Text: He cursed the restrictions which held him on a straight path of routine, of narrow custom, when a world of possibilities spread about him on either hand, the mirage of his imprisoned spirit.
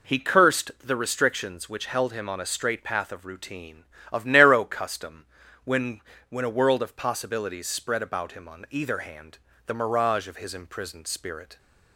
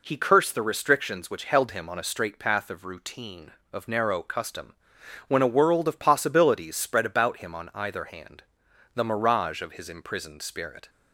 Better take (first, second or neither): second